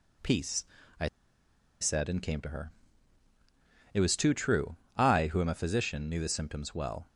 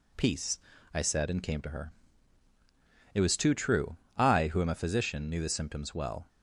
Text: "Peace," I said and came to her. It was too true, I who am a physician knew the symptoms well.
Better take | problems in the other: second | pauses between "I" and "said"; noticeable; at 1.0 s; 0.72 s long

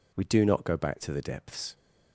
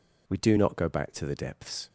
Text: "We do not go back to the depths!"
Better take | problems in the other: neither | none

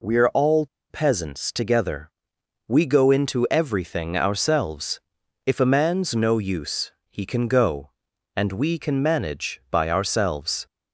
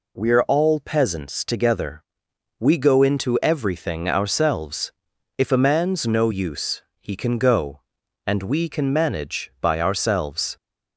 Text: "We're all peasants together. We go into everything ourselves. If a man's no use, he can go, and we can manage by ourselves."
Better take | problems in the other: second | pauses between "all" and "peasants"; slight; at 0.6 s; 0.23 s long

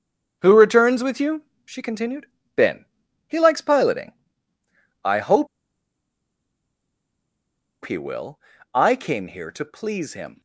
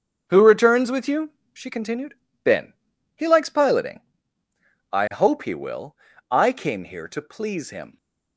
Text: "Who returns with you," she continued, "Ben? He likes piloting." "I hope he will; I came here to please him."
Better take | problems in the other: second | starts louder than the rest; until 1.4 s; 6.5 dB; also in the second // pauses between "hope" and "he"; strong; at 5.4 s; 2.3 s long

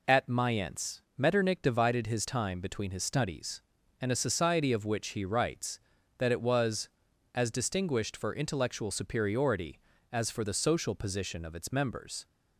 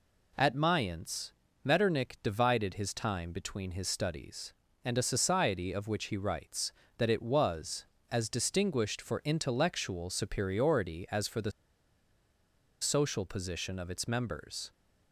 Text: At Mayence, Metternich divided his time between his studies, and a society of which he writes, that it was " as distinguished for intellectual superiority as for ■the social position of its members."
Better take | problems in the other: first | pauses between "the" and "social"; strong; at 11.5 s; 1.3 s long

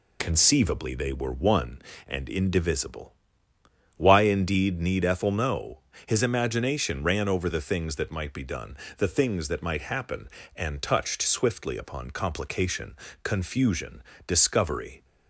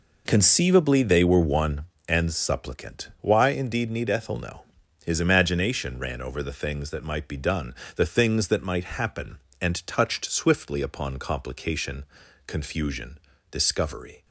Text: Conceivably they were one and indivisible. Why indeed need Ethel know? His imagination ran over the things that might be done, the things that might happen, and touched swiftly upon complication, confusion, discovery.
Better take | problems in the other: first | says "supplicant" for "indivisible"; at 2.3 s

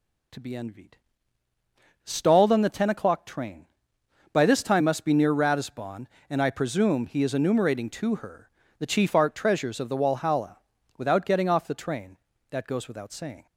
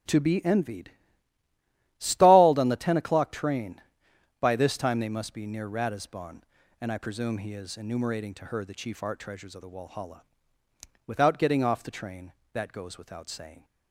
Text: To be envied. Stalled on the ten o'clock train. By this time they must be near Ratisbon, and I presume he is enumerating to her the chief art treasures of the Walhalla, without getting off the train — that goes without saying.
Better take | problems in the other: second | skips "they"; at 4.8 s // pauses between "her" and "the"; slight; at 8.4 s; 0.28 s long

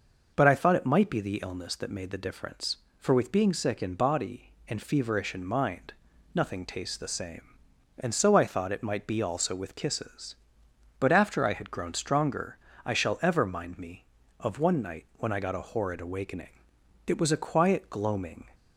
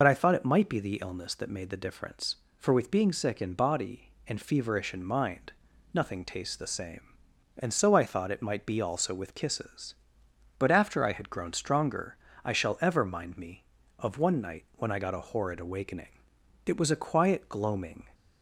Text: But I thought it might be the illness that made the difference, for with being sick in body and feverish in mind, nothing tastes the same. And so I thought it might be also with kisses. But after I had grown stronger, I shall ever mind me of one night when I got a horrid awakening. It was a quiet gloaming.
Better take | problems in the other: first | loses the start of "But"; at 0.0 s; 60 ms

